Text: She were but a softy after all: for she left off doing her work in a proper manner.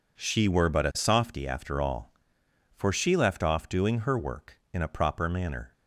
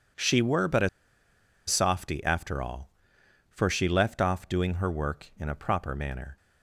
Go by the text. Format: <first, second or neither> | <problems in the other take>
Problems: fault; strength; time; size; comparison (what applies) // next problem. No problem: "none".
first | pauses between "a" and "softy"; noticeable; at 0.8 s; 0.79 s long